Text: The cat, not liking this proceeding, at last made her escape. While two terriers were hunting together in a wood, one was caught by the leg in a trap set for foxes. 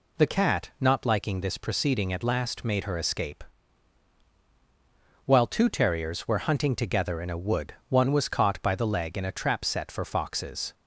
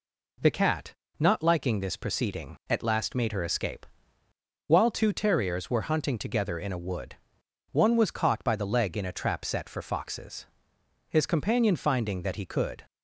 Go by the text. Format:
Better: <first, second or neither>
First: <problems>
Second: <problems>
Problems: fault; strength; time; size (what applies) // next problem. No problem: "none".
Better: first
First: none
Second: goes on to say "His companion finding that he could"; strong; from 11.0 s on; 1.7 s long